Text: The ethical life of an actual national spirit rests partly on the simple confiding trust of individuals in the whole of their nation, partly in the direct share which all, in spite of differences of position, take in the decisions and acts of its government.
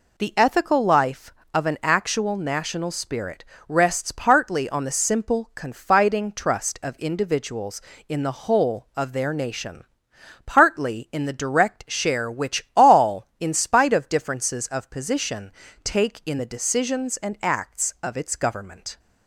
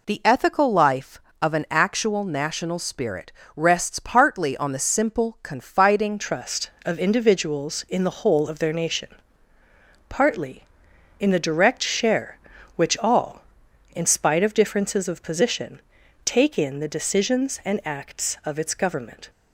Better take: first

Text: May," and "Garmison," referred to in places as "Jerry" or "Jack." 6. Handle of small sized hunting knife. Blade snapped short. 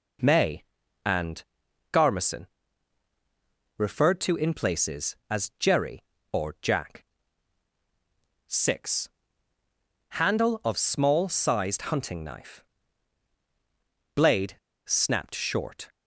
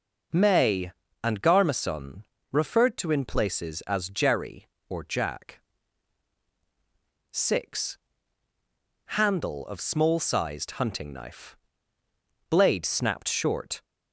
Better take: second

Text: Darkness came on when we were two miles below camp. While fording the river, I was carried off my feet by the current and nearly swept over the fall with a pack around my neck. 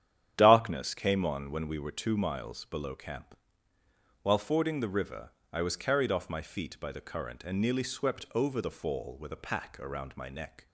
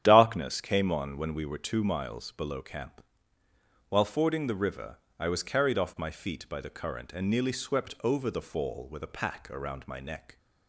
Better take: neither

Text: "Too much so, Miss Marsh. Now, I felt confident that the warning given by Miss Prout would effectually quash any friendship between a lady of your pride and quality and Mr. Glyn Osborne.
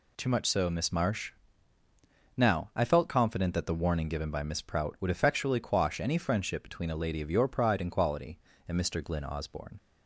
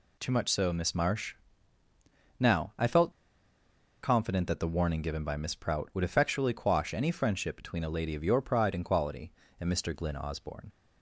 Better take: first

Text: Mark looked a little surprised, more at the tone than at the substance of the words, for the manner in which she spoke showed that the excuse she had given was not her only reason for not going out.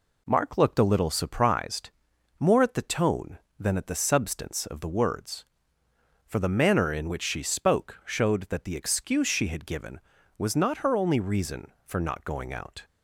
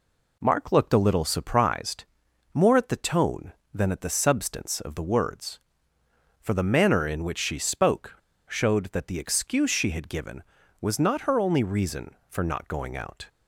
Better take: first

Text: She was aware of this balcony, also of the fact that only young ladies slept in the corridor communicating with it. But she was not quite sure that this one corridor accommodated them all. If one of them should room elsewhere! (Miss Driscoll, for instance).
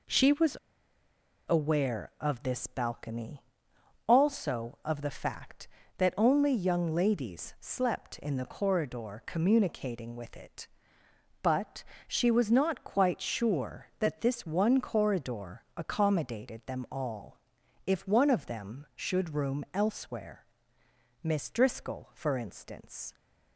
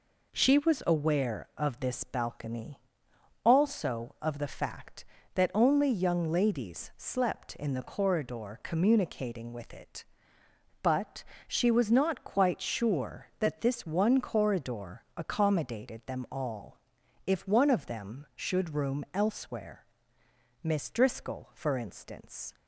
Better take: second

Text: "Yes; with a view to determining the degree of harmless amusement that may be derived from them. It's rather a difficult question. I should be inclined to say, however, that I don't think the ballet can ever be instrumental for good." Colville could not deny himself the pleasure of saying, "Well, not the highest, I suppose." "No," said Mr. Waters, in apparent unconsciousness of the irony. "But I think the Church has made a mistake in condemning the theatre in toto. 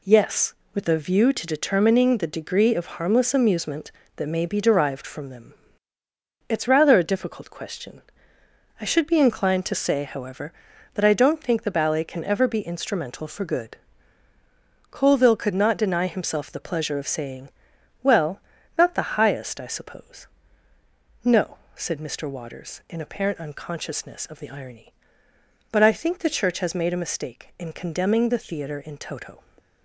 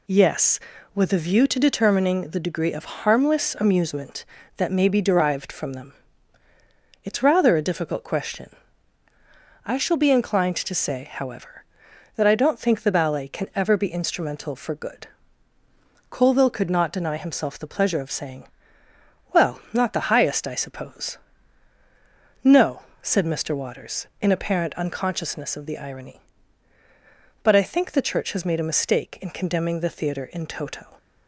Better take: first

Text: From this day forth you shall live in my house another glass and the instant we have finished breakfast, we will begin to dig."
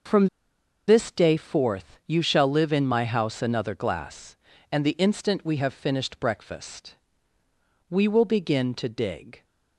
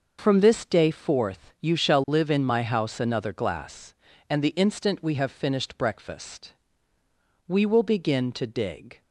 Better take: second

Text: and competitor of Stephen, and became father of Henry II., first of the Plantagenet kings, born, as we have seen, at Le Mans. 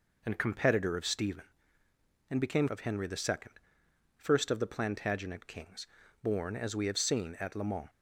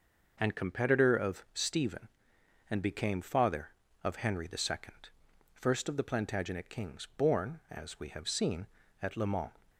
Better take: second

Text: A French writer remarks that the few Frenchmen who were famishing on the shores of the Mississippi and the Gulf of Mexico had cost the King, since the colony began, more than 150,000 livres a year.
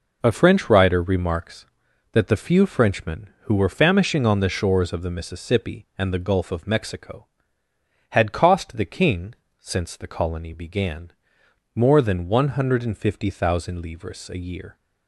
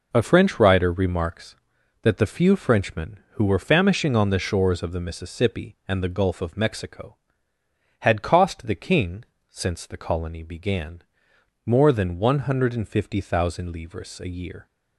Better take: neither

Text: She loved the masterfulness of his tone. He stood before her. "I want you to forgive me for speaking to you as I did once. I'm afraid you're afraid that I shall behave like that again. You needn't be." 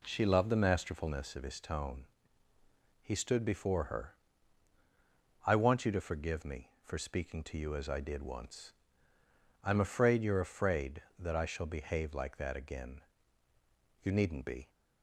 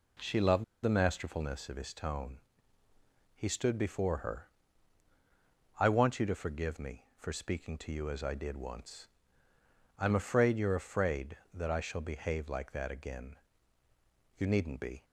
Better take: first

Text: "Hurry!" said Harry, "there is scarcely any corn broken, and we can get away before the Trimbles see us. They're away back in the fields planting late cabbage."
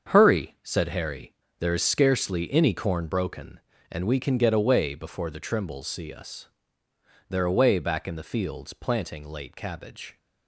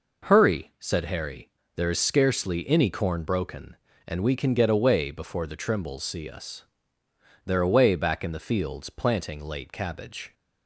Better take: second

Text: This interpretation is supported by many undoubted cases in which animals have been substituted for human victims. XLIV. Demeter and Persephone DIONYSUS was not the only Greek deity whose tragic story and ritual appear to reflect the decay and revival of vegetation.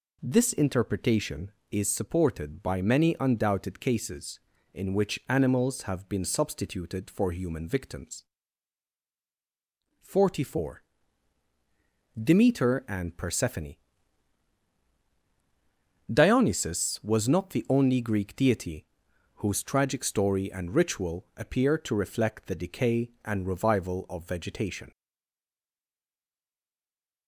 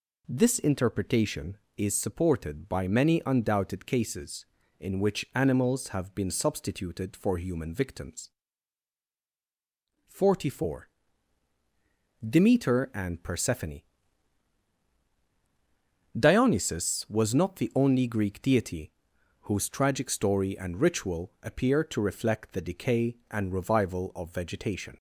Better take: second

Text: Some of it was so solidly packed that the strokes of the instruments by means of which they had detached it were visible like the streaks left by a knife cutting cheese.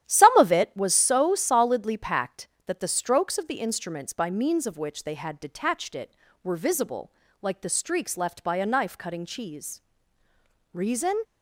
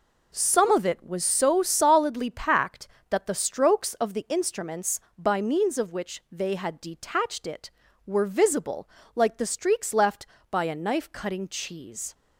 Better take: second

